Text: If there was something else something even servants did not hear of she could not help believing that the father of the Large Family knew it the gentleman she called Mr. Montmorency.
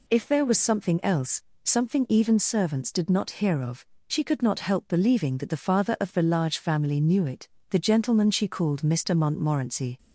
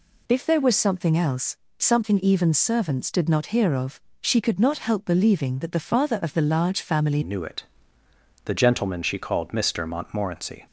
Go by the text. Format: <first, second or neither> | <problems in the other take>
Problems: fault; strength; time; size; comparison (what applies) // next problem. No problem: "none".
first | pauses between "else" and "something"; slight; at 1.5 s; 0.22 s long; slight in the first // pauses between "of" and "she"; slight; at 4.0 s; 0.20 s long; slight in the first // changes voice at "knew"; from 7.2 s on; 3.4 s long // pauses between "it" and "the"; noticeable; at 7.6 s; 0.80 s long; slight in the first